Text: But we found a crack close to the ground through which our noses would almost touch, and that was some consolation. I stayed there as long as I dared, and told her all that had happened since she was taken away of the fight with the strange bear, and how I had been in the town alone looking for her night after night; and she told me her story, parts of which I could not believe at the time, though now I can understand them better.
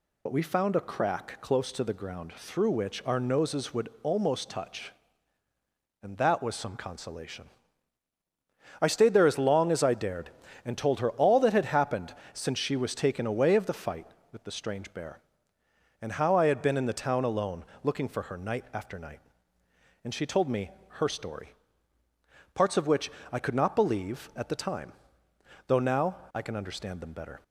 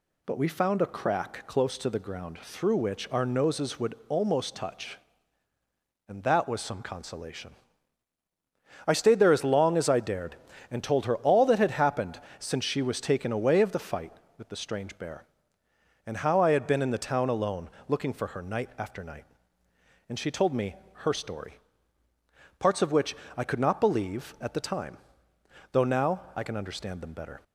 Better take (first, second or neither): second